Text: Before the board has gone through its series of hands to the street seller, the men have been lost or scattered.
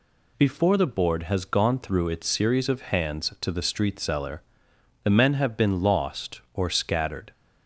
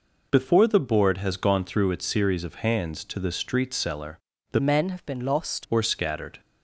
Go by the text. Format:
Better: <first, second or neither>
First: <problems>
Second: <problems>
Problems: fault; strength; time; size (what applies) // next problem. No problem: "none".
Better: first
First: none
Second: changes voice from "men" to "lost"; from 4.6 to 5.6 s; 1.0 s long